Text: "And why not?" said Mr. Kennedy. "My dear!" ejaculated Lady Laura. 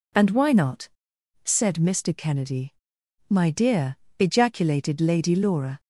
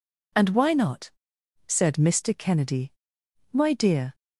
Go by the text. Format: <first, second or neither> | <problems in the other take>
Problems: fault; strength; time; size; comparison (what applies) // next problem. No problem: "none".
first | stops before "ejaculated Lady Laura"; at 4.1 s